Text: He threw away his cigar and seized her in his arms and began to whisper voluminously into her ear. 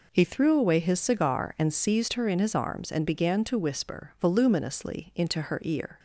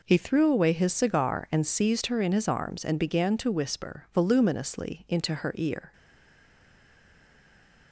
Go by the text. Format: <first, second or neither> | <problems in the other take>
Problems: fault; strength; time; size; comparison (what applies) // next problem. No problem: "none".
first | stays silent after the last word; noticeable; from 5.9 s on; 2.0 s long